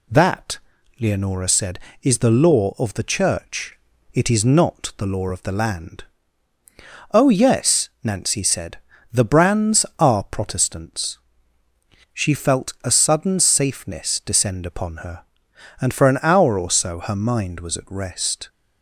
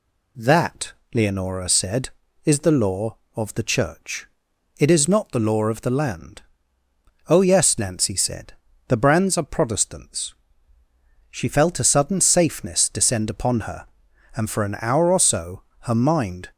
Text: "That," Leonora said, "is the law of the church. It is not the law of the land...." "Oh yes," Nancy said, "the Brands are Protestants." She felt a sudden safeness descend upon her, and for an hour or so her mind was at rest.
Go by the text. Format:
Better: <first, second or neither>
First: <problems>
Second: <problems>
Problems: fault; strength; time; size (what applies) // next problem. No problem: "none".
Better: first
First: none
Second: pauses between "so" and "her"; slight; at 15.6 s; 0.20 s long // stops before "was at rest"; at 16.5 s